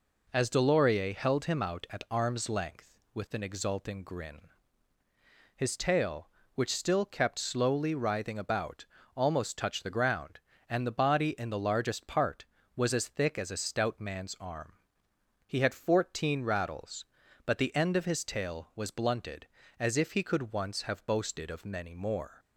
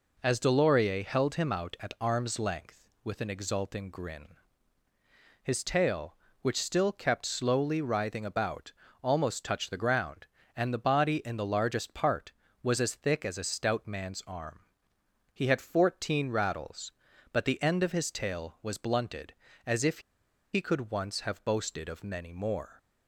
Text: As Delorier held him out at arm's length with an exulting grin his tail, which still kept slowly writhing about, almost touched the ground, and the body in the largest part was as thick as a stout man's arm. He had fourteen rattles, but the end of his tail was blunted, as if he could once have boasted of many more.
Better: first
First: pauses between "grin" and "his"; at 4.4 s; 1.1 s long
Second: pauses between "grin" and "his"; at 4.2 s; 1.1 s long // pauses between "if" and "he"; noticeable; at 20.0 s; 0.53 s long

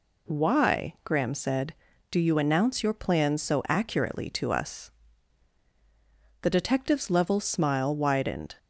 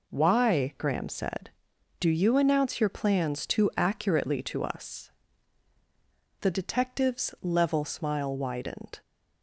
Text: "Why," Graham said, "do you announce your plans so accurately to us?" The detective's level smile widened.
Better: first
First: none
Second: says "too" for "so"; at 3.4 s

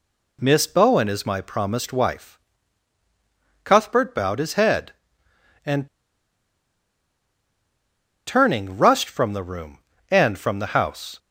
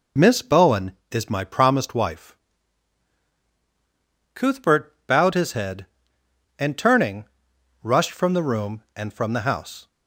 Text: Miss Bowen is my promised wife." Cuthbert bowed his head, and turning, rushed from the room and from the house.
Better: second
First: pauses between "and" and "turning"; strong; at 5.8 s; 2.4 s long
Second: none

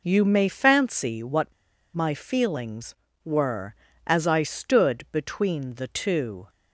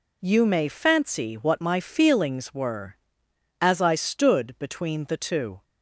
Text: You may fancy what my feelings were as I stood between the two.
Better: second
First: pauses between "what" and "my"; at 1.5 s; 0.42 s long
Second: none

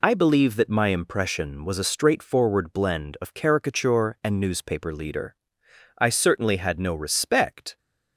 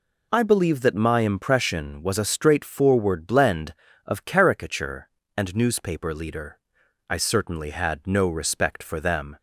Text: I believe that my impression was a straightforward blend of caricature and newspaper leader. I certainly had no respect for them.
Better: second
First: stops before "for them"; at 7.7 s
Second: none

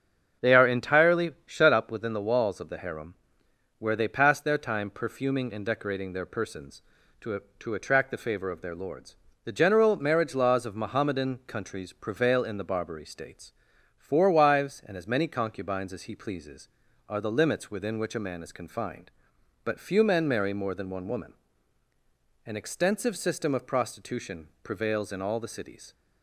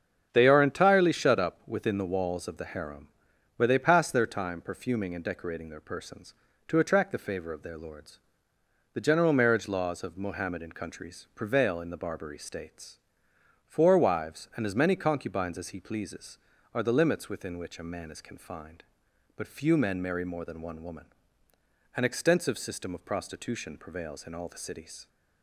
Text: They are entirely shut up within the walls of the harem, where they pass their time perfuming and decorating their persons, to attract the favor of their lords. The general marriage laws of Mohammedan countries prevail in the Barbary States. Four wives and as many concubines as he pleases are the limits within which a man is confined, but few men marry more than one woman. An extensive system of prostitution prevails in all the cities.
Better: second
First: starts louder than the rest; strong; until 1.5 s; 7.5 dB // says "to" twice; at 7.5 s // pauses between "prostitution" and "prevails"; slight; at 24.4 s; 0.16 s long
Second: starts louder than the rest; strong; until 1.3 s; 7.5 dB

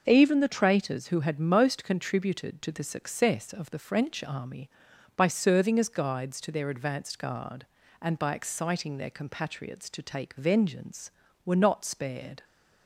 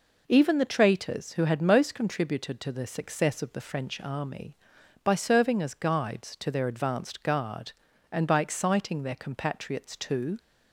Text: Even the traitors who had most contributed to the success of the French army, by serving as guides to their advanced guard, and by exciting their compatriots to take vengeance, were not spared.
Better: first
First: none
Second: stops before "take vengeance were not spared"; at 10.3 s

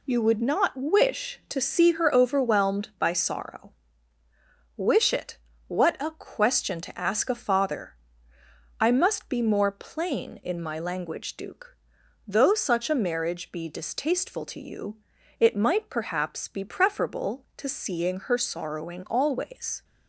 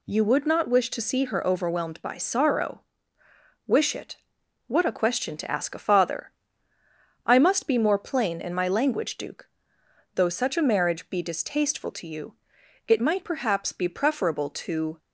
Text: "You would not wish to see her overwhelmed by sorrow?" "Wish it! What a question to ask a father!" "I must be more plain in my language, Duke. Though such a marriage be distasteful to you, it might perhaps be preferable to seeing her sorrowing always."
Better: first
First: none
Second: stops before "seeing her sorrowing always"; at 14.9 s

